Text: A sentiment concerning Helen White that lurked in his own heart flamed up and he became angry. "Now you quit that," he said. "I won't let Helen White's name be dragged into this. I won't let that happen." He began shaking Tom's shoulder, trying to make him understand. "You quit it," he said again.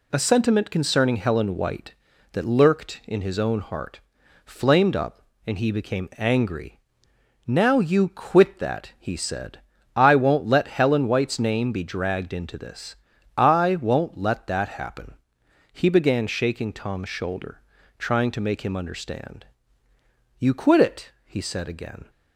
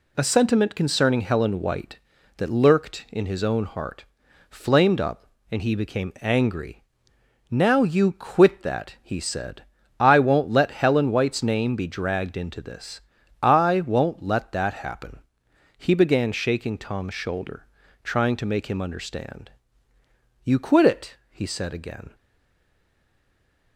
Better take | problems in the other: first | pauses between "heart" and "flamed"; at 4.0 s; 0.44 s long; also in the first // stays silent after the last word; noticeable; from 22.1 s on; 1.6 s long

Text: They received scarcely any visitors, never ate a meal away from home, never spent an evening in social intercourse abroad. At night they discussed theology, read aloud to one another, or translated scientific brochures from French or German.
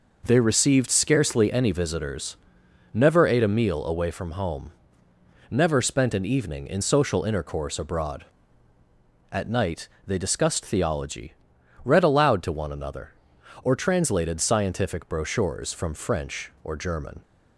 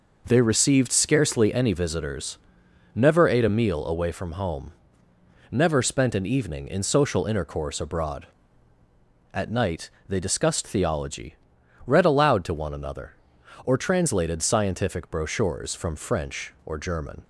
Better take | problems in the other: neither | pauses between "night" and "they"; slight; the same in both

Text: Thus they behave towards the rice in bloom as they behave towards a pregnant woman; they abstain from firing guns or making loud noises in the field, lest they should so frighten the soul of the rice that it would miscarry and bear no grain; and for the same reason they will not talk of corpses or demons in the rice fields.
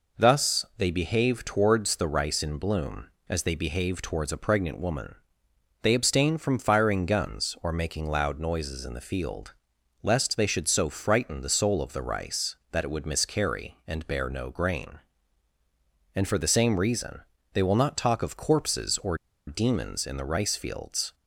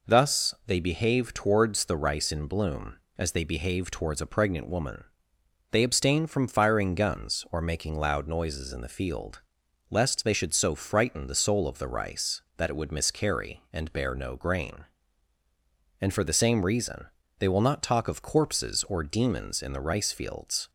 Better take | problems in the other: second | pauses between "reason" and "they"; slight; at 17.2 s; 0.32 s long; slight in the second // pauses between "or" and "demons"; slight; at 19.1 s; 0.30 s long

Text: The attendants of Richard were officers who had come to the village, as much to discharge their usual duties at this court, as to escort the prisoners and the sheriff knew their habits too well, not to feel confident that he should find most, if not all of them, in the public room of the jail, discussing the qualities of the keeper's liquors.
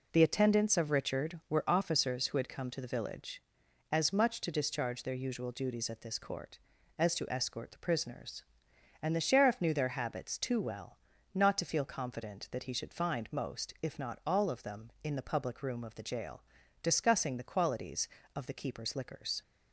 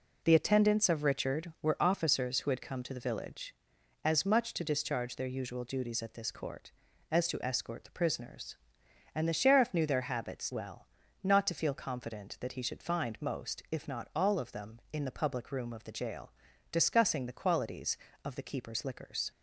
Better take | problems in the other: first | skips "too"; at 10.5 s

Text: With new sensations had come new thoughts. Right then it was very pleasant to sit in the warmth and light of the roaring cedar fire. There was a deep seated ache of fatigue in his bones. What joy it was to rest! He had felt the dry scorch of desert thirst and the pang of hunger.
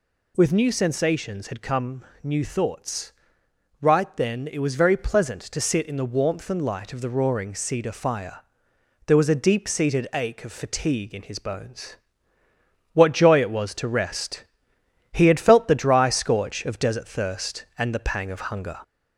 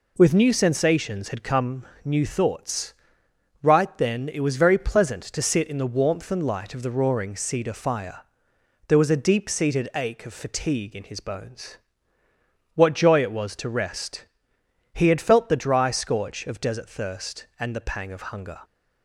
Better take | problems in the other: second | gets louder; slight; throughout; 2 dB // pauses between "come" and "new"; slight; at 2.0 s; 0.18 s long; slight in the second

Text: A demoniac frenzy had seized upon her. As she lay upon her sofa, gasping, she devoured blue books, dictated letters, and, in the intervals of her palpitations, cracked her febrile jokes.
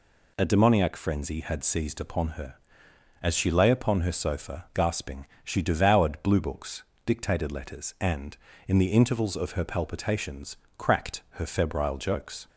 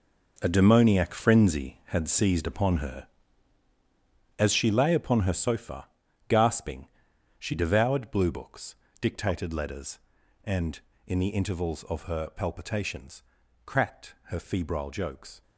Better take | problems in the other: first | gets quieter; strong; throughout; 11 dB

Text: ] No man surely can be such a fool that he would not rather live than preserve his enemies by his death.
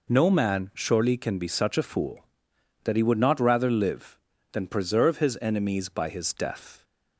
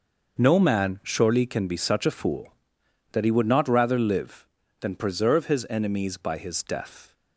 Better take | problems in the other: first | gets quieter; strong; throughout; 11.5 dB

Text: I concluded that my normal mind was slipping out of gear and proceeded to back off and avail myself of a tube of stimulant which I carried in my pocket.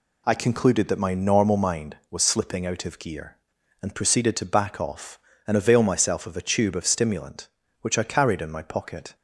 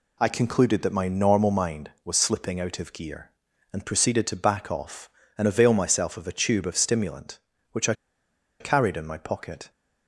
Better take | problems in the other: first | pauses between "I" and "carried"; noticeable; at 7.9 s; 0.66 s long

